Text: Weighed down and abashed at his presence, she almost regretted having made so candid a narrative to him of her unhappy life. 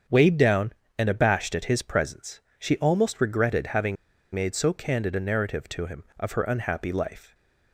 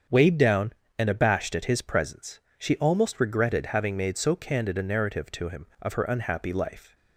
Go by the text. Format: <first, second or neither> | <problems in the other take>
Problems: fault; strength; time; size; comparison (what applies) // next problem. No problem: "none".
second | starts louder than the rest; strong; until 1.3 s; 7.5 dB; strong in the second // pauses between "having" and "made"; at 3.9 s; 0.38 s long